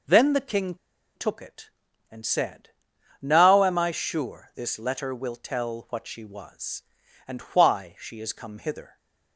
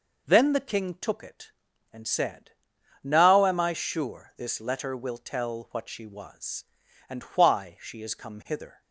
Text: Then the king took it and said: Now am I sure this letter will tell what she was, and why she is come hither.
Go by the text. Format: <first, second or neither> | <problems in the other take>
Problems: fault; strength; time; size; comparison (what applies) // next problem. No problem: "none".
second | pauses between "king" and "took"; at 0.7 s; 0.40 s long